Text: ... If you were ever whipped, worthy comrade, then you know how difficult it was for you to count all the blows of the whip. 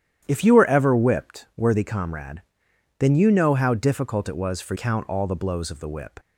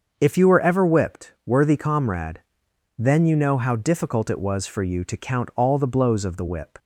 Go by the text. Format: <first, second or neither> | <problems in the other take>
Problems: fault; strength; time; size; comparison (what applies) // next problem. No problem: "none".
second | starts louder than the rest; strong; until 1.2 s; 10.5 dB; also in the second // skips "you to"; at 4.7 s